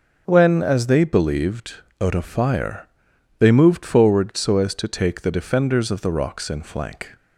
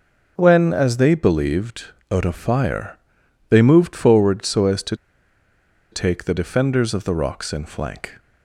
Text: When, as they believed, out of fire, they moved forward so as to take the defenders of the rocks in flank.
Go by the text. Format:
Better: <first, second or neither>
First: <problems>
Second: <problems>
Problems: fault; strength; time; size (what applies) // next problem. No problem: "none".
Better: first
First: none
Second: starts louder than the rest; until 1.3 s; 6 dB // pauses between "to" and "take"; noticeable; at 4.9 s; 0.97 s long